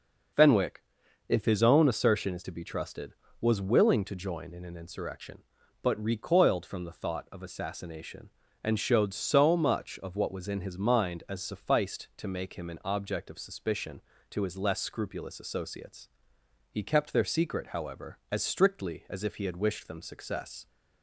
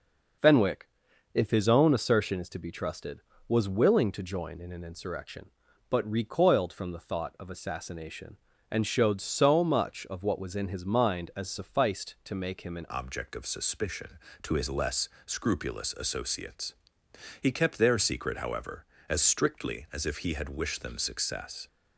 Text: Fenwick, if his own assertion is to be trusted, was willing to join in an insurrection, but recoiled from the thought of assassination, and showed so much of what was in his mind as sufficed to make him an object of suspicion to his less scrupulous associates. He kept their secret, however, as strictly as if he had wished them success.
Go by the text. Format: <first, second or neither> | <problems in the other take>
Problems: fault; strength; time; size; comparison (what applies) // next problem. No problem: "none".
first | changes voice at "object"; from 12.8 s on; 8.8 s long // pauses between "less" and "scrupulous"; slight; at 15.0 s; 0.16 s long